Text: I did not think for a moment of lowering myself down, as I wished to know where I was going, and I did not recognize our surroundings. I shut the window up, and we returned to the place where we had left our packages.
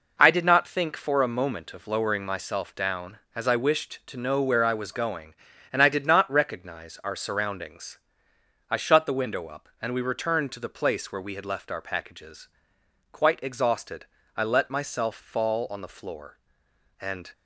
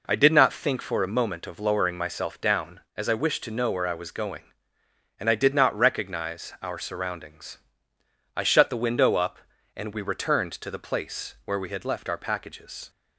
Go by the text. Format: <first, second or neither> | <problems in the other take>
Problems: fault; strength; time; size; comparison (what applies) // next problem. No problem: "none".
second | goes on to say "Quite exhausted I let myself fall on the floor and"; strong; from 13.1 s on; 4.2 s long